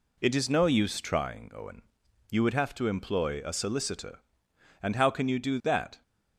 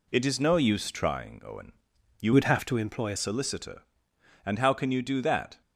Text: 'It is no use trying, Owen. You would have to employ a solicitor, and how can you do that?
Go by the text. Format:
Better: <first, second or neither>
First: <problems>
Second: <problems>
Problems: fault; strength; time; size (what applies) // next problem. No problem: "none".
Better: first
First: none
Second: changes voice from "would" to "a"; from 2.3 to 3.1 s; 0.8 s long